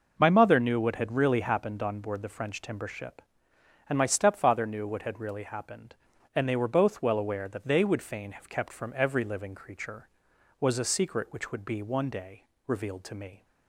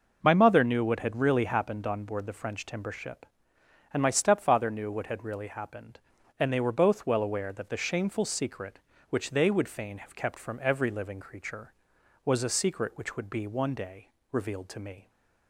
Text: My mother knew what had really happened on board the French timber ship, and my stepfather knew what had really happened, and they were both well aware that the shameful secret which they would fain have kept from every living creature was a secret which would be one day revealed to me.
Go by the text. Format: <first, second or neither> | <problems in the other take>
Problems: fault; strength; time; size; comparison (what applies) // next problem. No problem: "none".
second | skips "the shameful secret which"; at 7.6 s // pauses between "day" and "revealed"; slight; at 12.4 s; 0.24 s long; slight in the second